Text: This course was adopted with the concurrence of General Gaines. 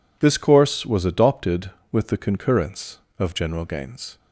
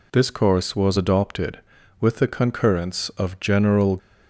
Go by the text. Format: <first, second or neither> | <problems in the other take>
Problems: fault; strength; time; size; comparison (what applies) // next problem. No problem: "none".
first | stops before "Gaines"; at 3.9 s